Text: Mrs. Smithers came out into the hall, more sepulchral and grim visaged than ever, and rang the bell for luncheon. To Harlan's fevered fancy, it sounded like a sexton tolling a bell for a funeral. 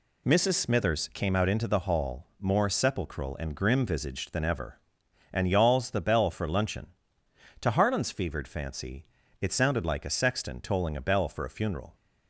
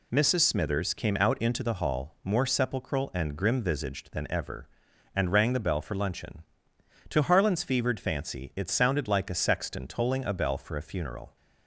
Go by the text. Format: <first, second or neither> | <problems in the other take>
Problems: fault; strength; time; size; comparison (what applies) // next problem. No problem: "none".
second | says "yawls" for "rang"; at 5.4 s